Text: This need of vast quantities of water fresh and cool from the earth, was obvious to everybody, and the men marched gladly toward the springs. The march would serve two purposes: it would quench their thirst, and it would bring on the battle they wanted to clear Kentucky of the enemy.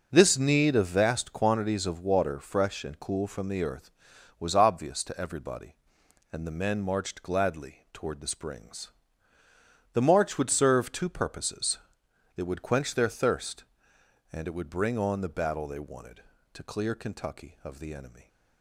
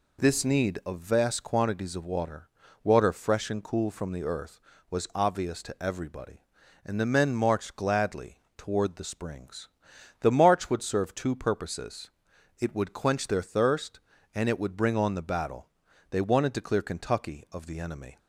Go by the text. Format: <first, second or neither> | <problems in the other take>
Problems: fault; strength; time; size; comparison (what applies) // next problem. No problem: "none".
first | says "water" twice; at 2.8 s // pauses between "gladly" and "toward"; slight; at 8.3 s; 0.16 s long // pauses between "battle" and "they"; at 15.6 s; 0.40 s long